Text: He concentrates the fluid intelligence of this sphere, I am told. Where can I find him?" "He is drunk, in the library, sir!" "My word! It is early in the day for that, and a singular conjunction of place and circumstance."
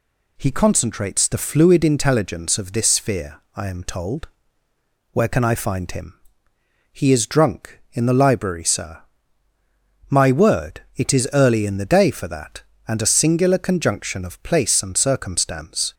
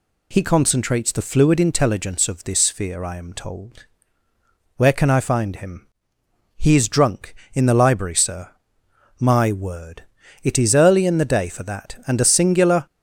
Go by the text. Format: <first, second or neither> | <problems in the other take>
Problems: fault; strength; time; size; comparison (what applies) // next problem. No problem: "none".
first | stops before "conjunction of place and circumstance"; at 12.8 s